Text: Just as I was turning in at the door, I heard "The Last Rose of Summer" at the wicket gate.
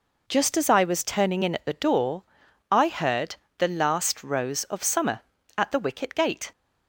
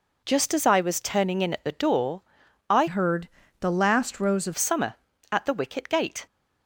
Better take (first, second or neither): first